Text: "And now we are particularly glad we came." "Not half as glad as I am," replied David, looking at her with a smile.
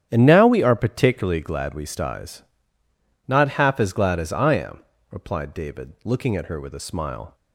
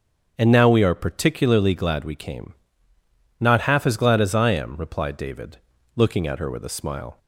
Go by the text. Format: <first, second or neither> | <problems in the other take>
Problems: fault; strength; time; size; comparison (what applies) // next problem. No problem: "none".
second | starts louder than the rest; strong; until 1.1 s; 9.5 dB; also in the second // says "styes" for "came"; at 1.8 s